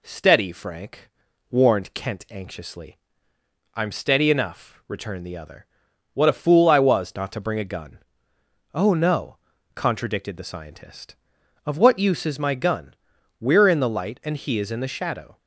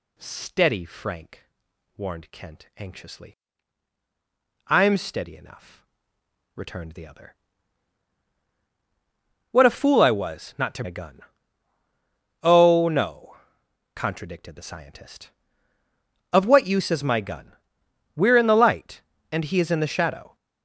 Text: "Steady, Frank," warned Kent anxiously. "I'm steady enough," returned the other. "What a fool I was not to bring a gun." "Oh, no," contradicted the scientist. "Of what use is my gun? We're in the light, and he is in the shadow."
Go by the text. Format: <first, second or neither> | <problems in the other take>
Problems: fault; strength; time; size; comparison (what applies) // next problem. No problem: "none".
first | skips "bring"; at 10.8 s